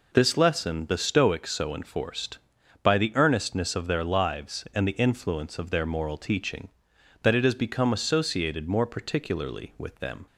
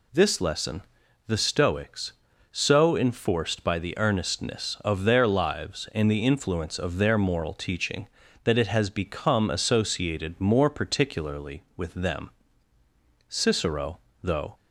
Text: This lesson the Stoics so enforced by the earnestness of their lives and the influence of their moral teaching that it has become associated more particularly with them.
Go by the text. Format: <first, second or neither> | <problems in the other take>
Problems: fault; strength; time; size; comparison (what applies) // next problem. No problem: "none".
first | pauses between "lesson" and "the"; noticeable; at 0.8 s; 0.46 s long // goes on to say "Cicero though"; noticeable; from 13.2 s on; 1.2 s long